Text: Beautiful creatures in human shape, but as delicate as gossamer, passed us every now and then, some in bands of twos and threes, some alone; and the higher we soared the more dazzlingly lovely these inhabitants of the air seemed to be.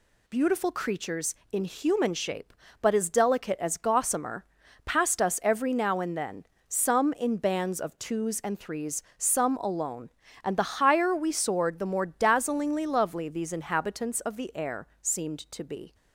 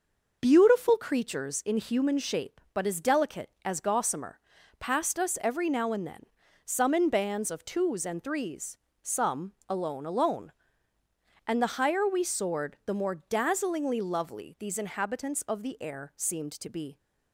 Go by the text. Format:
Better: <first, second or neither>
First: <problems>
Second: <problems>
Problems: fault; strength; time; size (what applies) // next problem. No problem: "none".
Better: first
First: none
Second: pauses between "some" and "alone"; slight; at 9.5 s; 0.16 s long // says "alone" twice; at 10.0 s